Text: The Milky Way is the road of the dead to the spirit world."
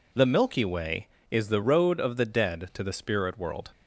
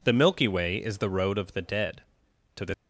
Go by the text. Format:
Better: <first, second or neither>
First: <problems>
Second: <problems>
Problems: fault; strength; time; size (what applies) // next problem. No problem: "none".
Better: first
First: none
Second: stops before "spirit world"; at 2.7 s